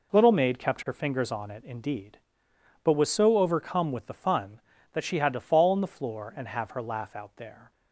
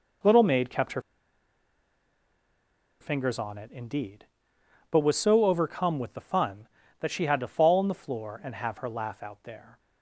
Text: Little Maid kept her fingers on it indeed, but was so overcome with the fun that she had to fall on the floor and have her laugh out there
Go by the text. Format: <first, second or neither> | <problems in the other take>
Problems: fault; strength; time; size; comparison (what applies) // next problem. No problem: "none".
first | pauses between "her" and "fingers"; strong; at 1.0 s; 1.9 s long